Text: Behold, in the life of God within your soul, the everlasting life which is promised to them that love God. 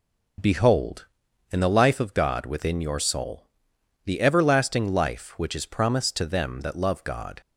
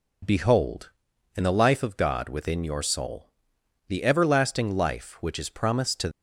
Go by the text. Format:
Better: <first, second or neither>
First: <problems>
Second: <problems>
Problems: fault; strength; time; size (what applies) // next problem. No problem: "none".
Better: first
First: none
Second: stops before "them that love God"; at 6.1 s